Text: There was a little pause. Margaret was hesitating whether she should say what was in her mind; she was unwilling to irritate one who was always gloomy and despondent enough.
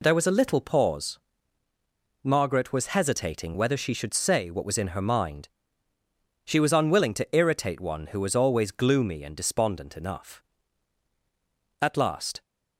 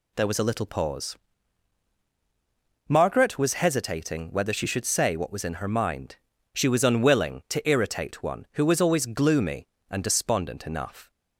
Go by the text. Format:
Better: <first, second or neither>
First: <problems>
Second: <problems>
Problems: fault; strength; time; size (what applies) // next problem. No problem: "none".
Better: second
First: goes on to say "At last"; noticeable; from 11.7 s on; 0.62 s long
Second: none